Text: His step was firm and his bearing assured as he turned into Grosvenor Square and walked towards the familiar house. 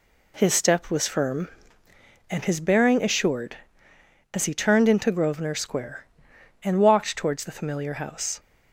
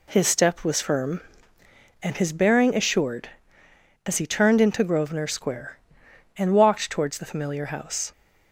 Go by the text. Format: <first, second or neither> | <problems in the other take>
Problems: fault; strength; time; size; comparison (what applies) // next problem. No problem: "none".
neither | none